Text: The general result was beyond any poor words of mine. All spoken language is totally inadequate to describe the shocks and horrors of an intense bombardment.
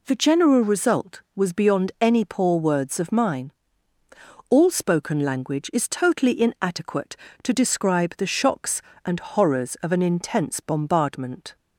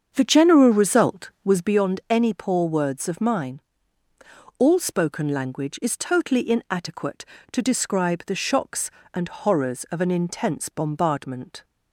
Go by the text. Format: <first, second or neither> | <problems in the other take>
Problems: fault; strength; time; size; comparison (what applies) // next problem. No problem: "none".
first | starts louder than the rest; strong; until 1.7 s; 7.5 dB